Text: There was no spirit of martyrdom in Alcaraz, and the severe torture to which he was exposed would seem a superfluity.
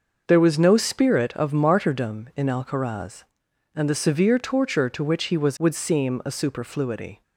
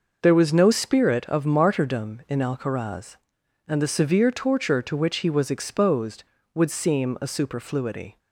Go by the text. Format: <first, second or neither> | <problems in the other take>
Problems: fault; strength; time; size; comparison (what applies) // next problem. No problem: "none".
second | skips "exposed"; at 5.5 s